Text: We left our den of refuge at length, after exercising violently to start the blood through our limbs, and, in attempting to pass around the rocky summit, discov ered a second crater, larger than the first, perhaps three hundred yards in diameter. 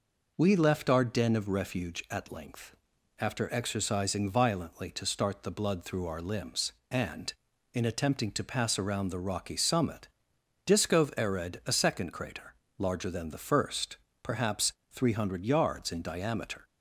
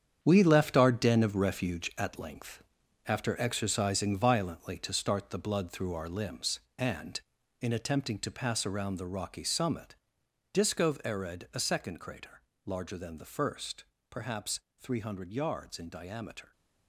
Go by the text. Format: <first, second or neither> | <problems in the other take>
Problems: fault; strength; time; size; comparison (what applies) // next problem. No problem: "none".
first | gets quieter; strong; throughout; 10 dB // pauses between "perhaps" and "three"; slight; at 14.5 s; 0.18 s long; slight in the first